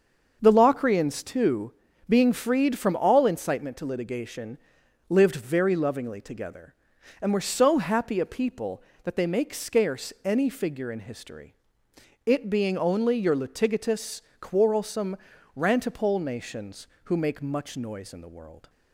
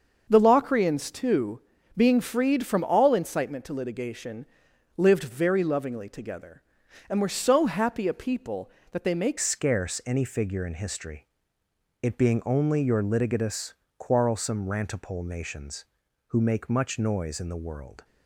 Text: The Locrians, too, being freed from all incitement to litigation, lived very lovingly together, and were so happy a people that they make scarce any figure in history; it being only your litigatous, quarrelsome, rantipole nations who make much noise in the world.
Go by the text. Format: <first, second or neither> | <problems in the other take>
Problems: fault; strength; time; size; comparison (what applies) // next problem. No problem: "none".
first | starts louder than the rest; until 1.3 s; 6.5 dB; also in the first // changes voice at "scarce"; from 9.3 s on; 8.7 s long